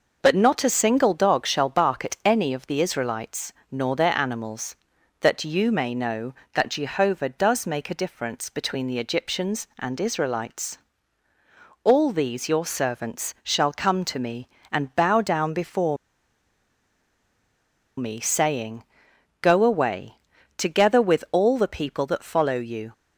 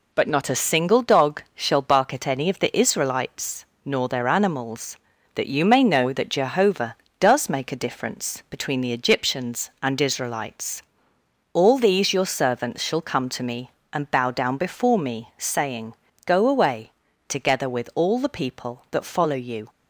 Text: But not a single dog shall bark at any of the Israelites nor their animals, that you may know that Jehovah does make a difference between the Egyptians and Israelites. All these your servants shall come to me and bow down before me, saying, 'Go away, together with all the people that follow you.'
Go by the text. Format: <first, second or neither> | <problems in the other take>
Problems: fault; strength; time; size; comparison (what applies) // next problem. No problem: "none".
second | pauses between "Israelites" and "nor"; slight; at 3.5 s; 0.18 s long; slight in the second // pauses between "before" and "me"; strong; at 15.9 s; 2.0 s long